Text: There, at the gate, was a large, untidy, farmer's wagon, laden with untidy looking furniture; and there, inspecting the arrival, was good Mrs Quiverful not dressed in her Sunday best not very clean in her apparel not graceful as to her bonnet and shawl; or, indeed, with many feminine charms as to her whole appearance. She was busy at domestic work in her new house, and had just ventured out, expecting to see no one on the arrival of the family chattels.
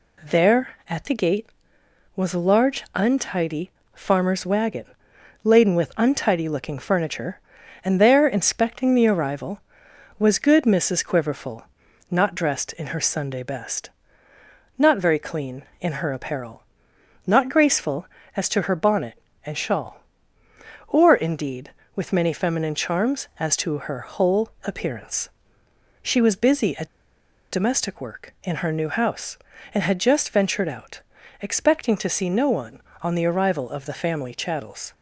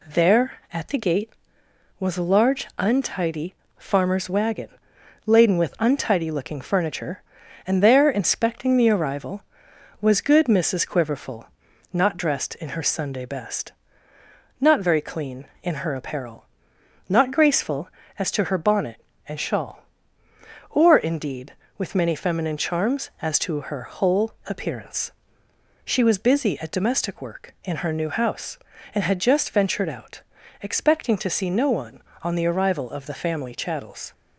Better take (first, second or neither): second